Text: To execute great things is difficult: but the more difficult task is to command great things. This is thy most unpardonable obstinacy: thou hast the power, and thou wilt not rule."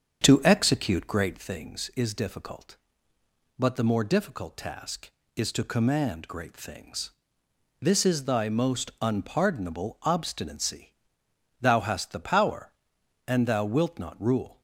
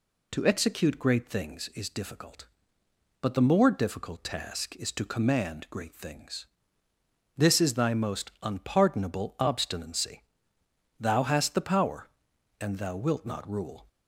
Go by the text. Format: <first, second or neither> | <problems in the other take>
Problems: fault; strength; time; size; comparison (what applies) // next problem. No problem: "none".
second | starts louder than the rest; strong; until 1.5 s; 7.5 dB